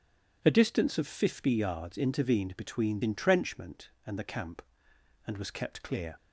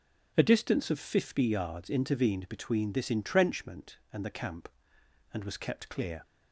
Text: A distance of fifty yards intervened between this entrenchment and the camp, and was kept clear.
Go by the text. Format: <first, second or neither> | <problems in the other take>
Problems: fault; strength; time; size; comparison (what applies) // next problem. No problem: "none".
second | skips "this"; at 3.0 s